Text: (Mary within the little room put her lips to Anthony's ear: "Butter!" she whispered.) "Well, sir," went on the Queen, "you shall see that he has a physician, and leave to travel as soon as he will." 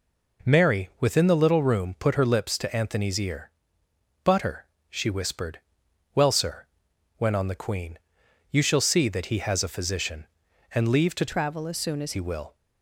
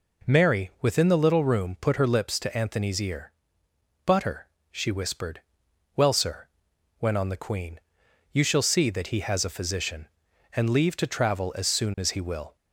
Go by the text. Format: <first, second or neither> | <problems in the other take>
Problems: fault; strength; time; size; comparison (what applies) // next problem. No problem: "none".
second | changes voice from "travel" to "as"; from 11.2 to 12.1 s; 0.9 s long